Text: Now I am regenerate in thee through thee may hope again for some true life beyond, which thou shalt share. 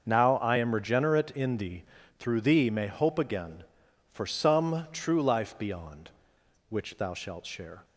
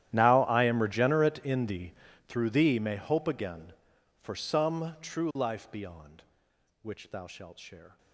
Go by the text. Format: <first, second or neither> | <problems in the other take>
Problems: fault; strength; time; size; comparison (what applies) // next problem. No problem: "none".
first | gets quieter; strong; throughout; 22.5 dB // starts louder than the rest; strong; until 1.1 s; 12 dB; also in the first // pauses between "thee" and "through"; slight; at 1.9 s; 0.34 s long; slight in the first